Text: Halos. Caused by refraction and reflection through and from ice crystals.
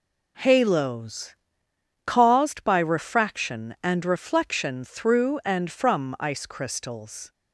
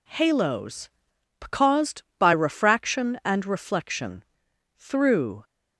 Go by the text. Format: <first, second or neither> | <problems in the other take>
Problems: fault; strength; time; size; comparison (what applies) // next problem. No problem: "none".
first | pauses between "reflection" and "through"; noticeable; at 4.2 s; 0.54 s long // stops before "and from ice crystals"; at 5.4 s